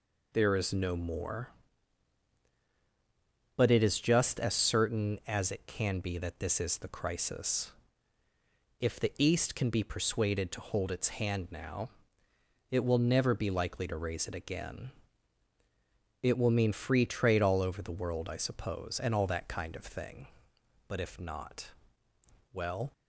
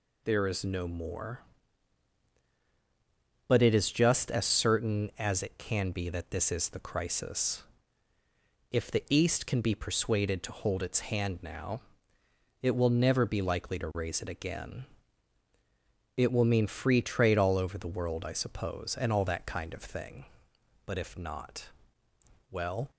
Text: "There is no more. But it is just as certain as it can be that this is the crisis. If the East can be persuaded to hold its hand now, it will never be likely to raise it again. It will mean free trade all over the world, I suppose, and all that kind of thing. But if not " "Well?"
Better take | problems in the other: second | starts louder than the rest; slight; until 1.7 s; 3 dB

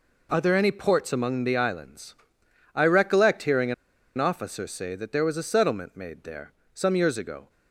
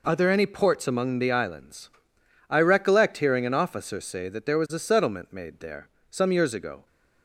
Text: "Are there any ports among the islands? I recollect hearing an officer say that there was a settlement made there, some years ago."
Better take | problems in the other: second | pauses between "hearing" and "an"; at 3.7 s; 0.43 s long

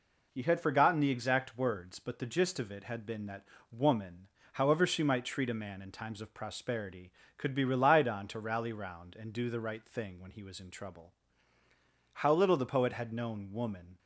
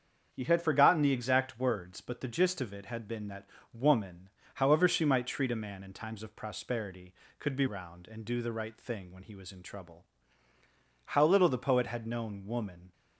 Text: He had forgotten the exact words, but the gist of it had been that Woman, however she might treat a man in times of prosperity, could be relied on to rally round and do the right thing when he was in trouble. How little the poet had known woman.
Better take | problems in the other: first | starts louder than the rest; strong; until 1.3 s; 7.5 dB // pauses between "that" and "Woman"; slight; at 3.4 s; 0.26 s long; slight in the first // skips "relied on to rally"; at 7.6 s

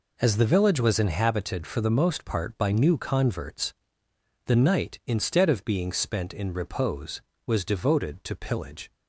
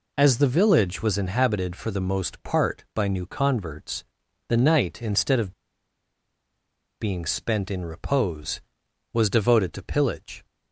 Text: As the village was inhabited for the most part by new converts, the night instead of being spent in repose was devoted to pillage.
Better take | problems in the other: first | pauses between "of" and "being"; strong; at 5.5 s; 1.4 s long

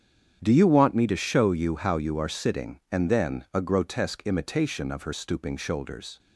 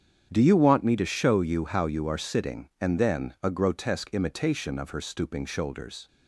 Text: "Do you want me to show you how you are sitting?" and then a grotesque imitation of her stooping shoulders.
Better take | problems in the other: neither | starts louder than the rest; strong; the same in both

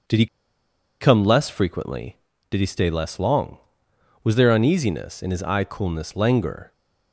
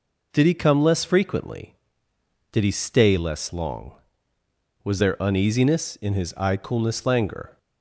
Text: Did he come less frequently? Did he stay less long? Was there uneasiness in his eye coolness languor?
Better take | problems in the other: second | pauses between "he" and "come"; noticeable; at 0.2 s; 0.74 s long

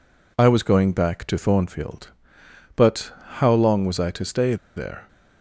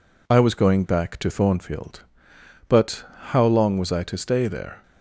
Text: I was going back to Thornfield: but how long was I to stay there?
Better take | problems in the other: second | pauses between "but" and "how"; slight; at 3.1 s; 0.24 s long; slight in the second // pauses between "stay" and "there"; slight; at 4.5 s; 0.20 s long

